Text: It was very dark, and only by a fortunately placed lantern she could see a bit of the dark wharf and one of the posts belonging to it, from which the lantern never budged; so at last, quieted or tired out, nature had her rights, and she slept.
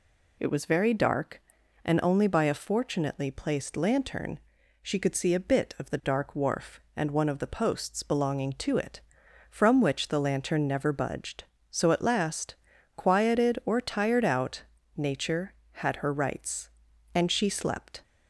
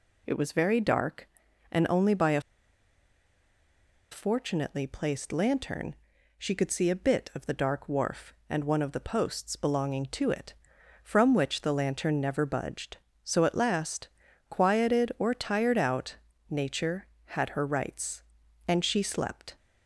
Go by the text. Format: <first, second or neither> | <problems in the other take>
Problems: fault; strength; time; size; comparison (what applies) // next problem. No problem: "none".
first | pauses between "a" and "fortunately"; strong; at 2.4 s; 1.7 s long // pauses between "lantern" and "she"; at 5.9 s; 0.42 s long; also in the first